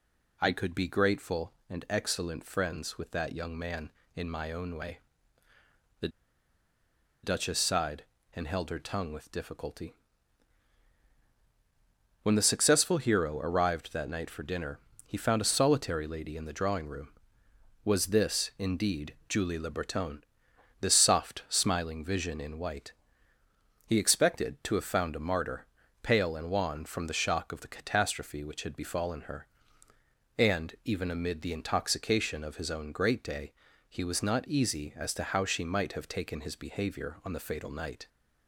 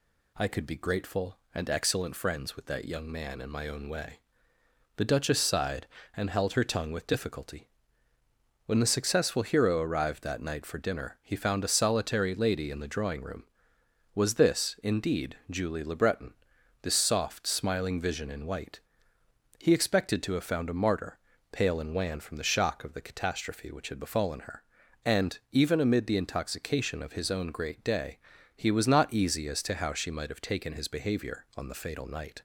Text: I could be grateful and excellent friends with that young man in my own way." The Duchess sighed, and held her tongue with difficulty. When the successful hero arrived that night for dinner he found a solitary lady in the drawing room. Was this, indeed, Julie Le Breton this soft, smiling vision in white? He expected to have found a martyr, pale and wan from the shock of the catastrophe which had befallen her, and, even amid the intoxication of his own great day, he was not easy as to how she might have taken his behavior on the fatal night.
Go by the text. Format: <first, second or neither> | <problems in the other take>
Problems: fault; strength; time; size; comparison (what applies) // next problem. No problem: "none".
second | pauses between "The" and "Duchess"; at 6.0 s; 1.1 s long // pauses between "dinner" and "he"; slight; at 14.7 s; 0.28 s long // pauses between "Breton" and "this"; noticeable; at 20.2 s; 0.60 s long; noticeable in the second